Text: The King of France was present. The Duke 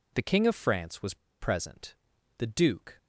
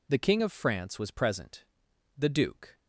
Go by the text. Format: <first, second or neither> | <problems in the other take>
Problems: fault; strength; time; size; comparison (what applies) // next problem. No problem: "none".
second | pauses between "was" and "present"; slight; at 1.1 s; 0.25 s long